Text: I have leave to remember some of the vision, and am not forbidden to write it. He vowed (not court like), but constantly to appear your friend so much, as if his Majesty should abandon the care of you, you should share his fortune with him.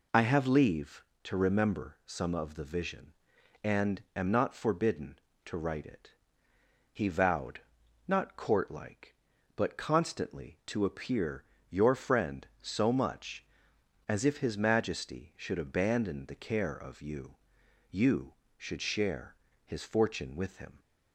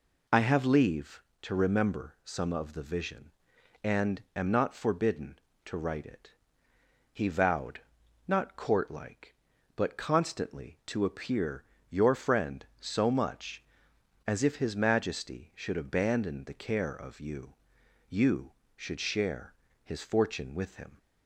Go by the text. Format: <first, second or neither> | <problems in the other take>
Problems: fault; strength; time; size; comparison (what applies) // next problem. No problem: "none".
neither | pauses between "appear" and "your"; slight; the same in both // pauses between "share" and "his"; slight; the same in both